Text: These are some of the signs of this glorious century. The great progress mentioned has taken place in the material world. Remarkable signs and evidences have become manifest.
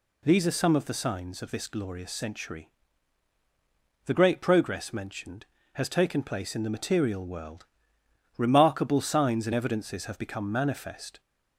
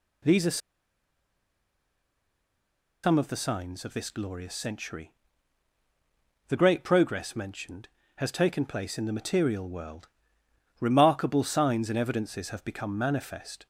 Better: first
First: none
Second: pauses between "are" and "some"; strong; at 0.5 s; 2.4 s long

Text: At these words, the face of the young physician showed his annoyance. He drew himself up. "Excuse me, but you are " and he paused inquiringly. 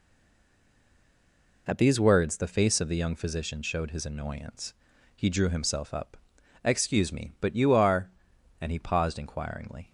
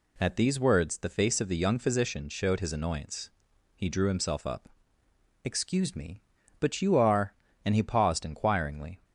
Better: second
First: stays silent before the first word; noticeable; until 1.6 s; 1.6 s long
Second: none

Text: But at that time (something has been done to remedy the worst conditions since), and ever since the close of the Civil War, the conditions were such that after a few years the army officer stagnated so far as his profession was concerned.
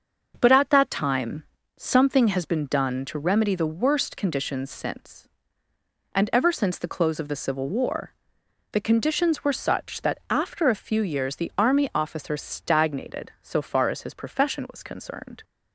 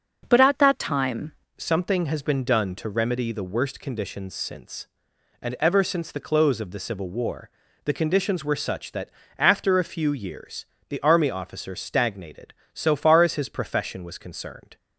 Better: first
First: starts louder than the rest; until 1.4 s; 6.5 dB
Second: starts louder than the rest; noticeable; until 1.2 s; 6 dB // changes voice at "something"; from 1.5 s on; 13.2 s long // pauses between "that" and "after"; slight; at 9.0 s; 0.30 s long // pauses between "years" and "the"; slight; at 10.6 s; 0.24 s long

